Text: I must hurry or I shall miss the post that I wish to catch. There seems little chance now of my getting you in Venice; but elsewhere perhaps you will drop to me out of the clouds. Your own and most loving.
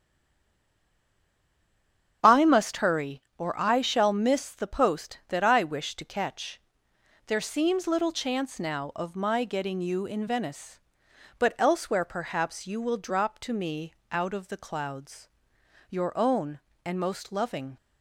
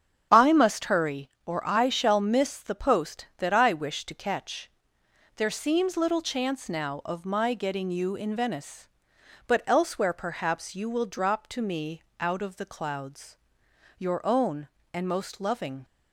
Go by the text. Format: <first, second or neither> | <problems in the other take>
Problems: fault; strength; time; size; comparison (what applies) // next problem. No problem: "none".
second | stays silent before the first word; until 2.2 s; 2.2 s long // starts louder than the rest; strong; until 3.2 s; 7.5 dB; strong in the second // pauses between "me" and "out"; slight; at 13.9 s; 0.18 s long; slight in the second